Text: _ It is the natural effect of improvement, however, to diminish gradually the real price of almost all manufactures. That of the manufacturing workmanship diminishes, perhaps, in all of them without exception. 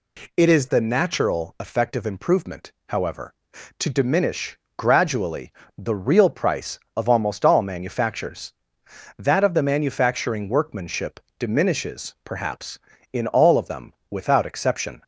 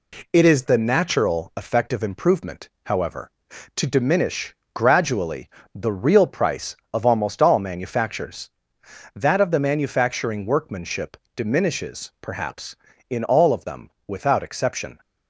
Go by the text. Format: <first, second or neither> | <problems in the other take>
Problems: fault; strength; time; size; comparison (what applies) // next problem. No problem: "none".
first | gets quieter; slight; throughout; 3.5 dB // pauses between "diminish" and "gradually"; slight; at 4.5 s; 0.22 s long; slight in the first // pauses between "gradually" and "the"; slight; at 5.4 s; 0.24 s long; slight in the first // pauses between "workmanship" and "diminishes"; slight; at 11.1 s; 0.18 s long; slight in the first // pauses between "them" and "without"; slight; at 13.8 s; 0.16 s long; slight in the first